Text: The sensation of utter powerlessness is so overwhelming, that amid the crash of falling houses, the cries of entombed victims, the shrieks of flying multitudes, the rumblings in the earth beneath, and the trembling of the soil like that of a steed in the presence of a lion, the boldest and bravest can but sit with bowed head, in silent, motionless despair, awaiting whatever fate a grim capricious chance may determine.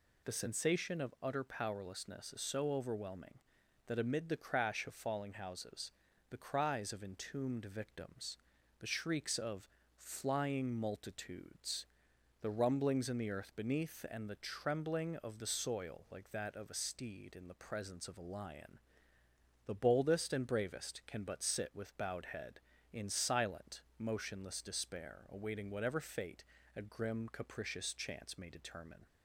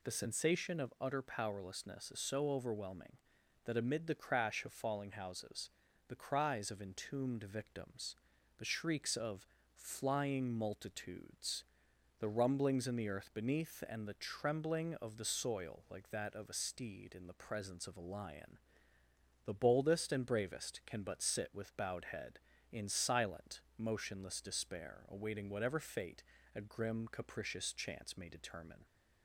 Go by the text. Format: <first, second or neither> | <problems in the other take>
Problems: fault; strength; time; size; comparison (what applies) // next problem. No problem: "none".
neither | pauses between "of" and "flying"; slight; the same in both // pauses between "fate" and "a"; slight; the same in both